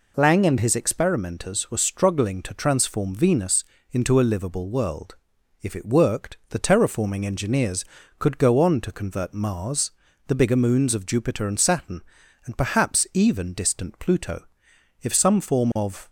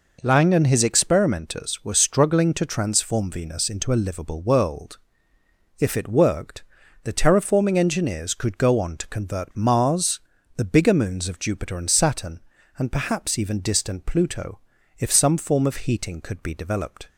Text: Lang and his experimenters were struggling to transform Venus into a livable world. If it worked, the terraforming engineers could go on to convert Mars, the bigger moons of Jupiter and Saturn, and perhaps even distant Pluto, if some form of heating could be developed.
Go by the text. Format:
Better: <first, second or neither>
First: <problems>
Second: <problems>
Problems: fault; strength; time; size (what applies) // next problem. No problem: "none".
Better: second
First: pauses between "Venus" and "into"; slight; at 3.6 s; 0.26 s long // stops before "heating could be developed"; at 16.0 s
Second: none